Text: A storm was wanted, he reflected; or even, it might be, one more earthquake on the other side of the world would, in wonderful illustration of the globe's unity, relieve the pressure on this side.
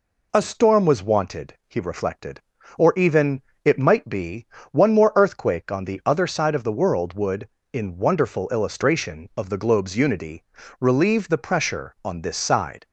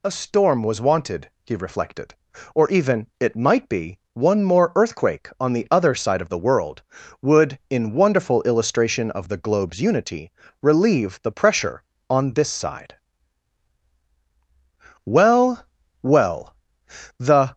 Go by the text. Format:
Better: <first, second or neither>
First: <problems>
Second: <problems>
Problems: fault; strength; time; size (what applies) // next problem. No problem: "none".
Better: first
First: none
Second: goes on to say "Well well the"; strong; from 15.0 s on; 2.4 s long